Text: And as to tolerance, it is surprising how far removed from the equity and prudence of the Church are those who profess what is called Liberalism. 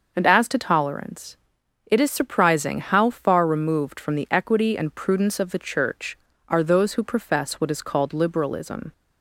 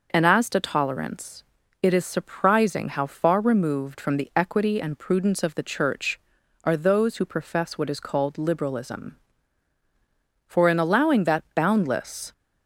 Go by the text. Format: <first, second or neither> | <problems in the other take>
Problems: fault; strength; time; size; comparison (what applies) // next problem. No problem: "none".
first | goes on to say "For in allowing that boundless"; strong; from 10.4 s on; 1.8 s long